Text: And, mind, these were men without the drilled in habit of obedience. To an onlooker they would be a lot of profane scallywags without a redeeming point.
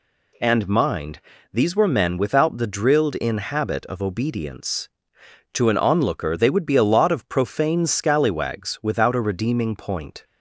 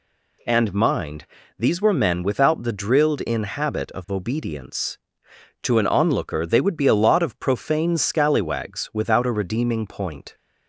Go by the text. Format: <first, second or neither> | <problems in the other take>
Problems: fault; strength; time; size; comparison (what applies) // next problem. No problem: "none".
neither | none